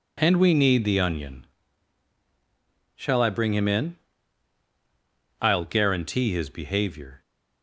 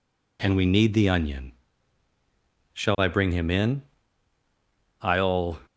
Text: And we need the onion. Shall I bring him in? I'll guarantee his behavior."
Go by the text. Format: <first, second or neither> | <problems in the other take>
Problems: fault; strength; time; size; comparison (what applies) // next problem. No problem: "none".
first | stops before "guarantee his behavior"; at 5.6 s